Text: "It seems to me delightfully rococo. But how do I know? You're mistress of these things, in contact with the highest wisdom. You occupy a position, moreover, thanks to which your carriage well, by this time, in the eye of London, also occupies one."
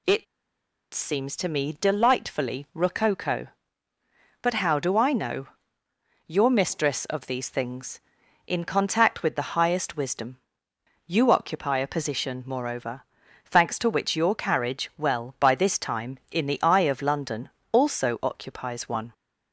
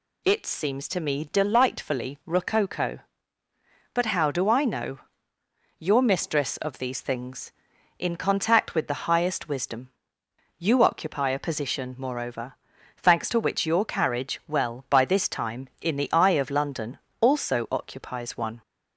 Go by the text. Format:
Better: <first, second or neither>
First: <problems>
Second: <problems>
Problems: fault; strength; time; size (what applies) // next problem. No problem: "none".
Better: second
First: pauses between "It" and "seems"; noticeable; at 0.2 s; 0.69 s long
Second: none